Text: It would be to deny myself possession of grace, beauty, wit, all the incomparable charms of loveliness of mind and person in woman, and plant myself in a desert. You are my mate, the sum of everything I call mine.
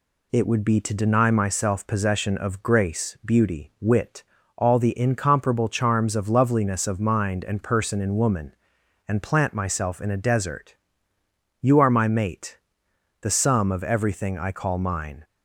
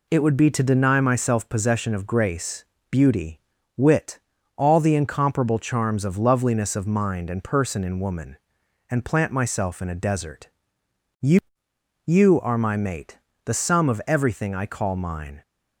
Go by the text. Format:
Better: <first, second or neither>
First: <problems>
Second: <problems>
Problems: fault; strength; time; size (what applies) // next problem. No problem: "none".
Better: first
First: none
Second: says "You" twice; at 12.0 s